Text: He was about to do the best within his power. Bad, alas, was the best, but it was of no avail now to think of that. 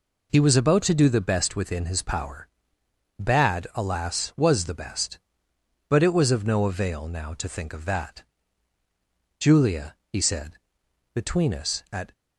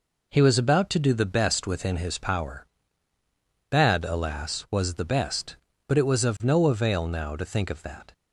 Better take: second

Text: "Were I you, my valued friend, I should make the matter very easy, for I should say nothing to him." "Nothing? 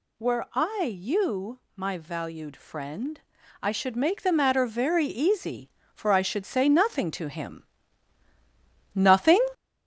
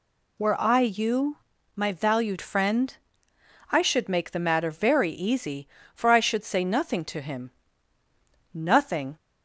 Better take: second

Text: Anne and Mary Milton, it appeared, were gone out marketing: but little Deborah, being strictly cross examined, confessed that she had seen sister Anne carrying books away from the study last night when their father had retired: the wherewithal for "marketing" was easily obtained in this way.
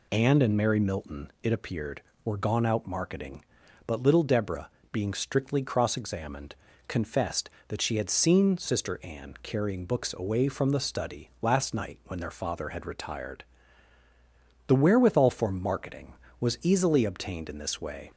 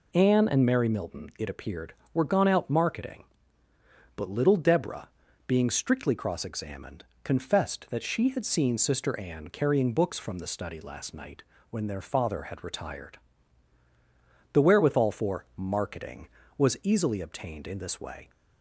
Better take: first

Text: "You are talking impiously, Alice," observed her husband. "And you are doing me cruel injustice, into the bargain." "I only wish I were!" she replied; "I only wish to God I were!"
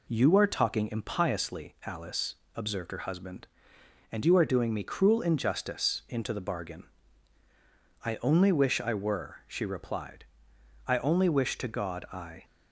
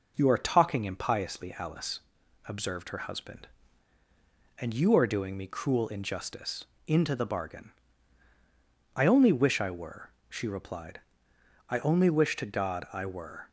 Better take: second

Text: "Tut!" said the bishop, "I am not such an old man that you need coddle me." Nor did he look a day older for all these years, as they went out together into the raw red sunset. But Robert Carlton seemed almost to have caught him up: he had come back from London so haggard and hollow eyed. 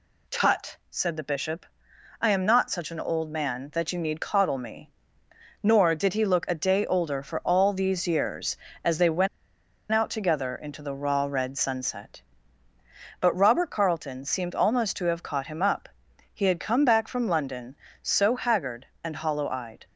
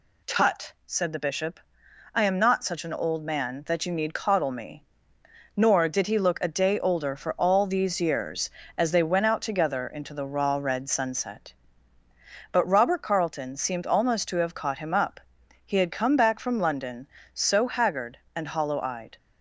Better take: second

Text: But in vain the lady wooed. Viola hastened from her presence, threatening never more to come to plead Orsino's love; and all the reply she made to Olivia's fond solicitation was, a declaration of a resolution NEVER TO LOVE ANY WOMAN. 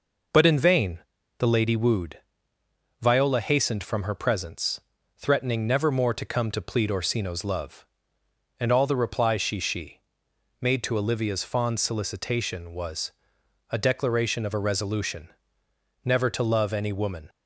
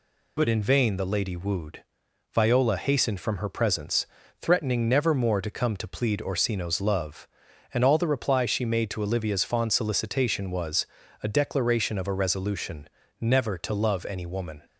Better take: second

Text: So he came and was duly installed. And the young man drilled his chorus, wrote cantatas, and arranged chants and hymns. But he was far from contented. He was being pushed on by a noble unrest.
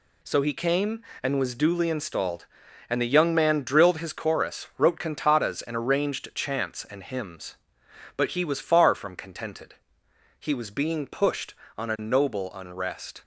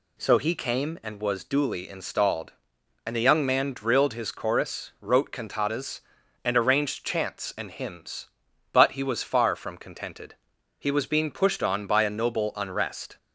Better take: second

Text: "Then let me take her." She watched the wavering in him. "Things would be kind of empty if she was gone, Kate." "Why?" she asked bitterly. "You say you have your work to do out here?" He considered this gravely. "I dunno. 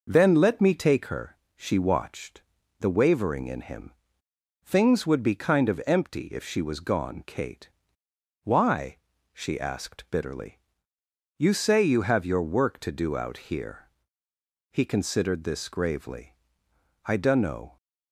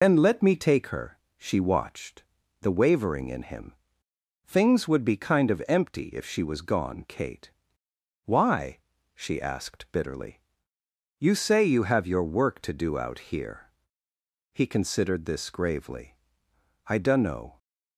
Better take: first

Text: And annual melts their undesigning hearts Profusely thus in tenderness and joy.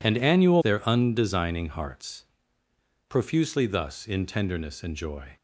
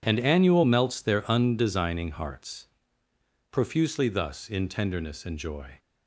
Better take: second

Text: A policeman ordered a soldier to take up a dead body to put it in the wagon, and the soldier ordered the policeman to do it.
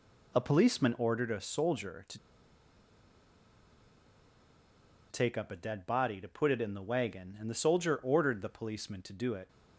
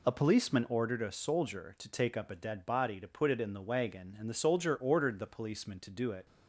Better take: second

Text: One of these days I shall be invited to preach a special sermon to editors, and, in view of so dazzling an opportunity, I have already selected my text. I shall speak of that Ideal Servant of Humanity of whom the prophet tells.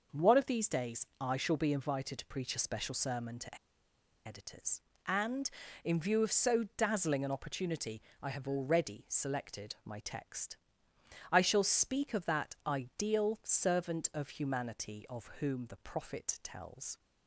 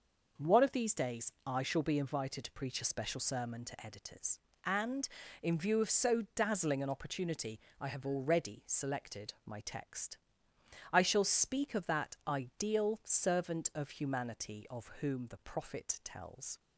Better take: second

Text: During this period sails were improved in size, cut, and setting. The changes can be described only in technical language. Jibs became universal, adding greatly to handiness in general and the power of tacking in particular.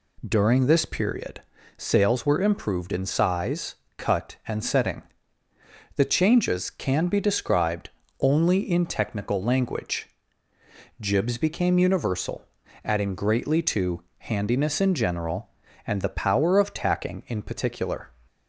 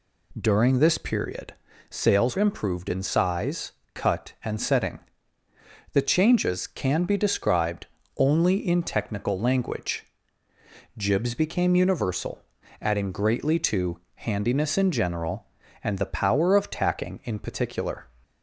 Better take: first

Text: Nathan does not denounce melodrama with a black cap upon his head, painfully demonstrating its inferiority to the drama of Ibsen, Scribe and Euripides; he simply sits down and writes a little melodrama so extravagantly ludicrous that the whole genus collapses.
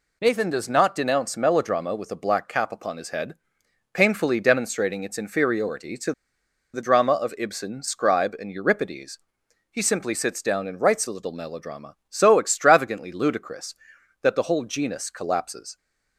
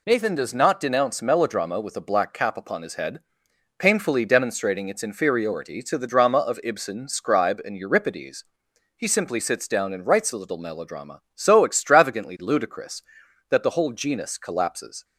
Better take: second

